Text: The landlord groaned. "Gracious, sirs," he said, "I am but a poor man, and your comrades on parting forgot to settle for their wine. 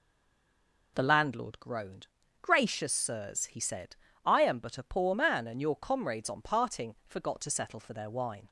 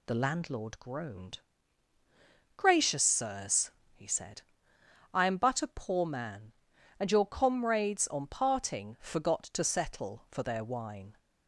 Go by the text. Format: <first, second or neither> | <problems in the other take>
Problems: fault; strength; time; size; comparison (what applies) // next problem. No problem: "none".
second | stays silent before the first word; slight; until 0.9 s; 0.9 s long